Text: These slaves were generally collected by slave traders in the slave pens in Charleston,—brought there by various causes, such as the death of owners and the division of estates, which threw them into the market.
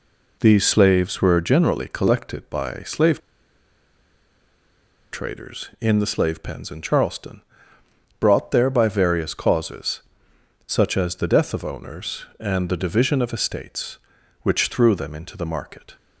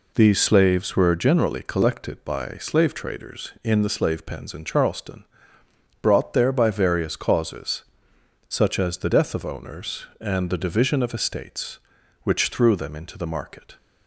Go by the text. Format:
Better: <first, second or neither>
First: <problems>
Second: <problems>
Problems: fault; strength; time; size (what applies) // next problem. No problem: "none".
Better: second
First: pauses between "slave" and "traders"; strong; at 3.1 s; 1.9 s long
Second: none